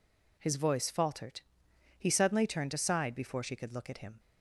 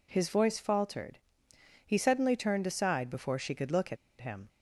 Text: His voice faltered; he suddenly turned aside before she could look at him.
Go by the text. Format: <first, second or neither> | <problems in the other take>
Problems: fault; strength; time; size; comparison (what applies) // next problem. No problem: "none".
first | pauses between "at" and "him"; slight; at 3.9 s; 0.24 s long